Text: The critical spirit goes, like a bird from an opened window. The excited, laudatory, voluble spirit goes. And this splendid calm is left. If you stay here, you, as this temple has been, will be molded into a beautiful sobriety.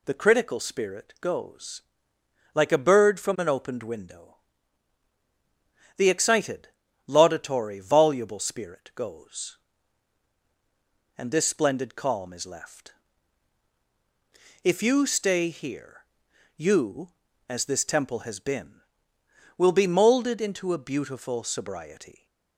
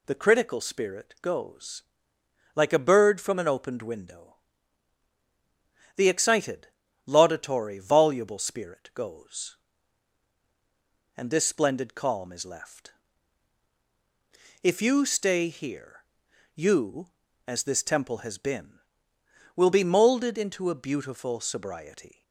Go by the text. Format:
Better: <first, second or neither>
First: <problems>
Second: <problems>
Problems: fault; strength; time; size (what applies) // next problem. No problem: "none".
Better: neither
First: none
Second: none